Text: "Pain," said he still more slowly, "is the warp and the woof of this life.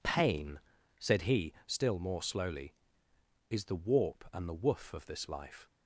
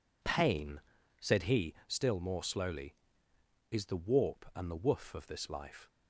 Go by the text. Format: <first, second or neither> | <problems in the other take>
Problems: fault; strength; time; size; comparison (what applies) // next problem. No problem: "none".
neither | none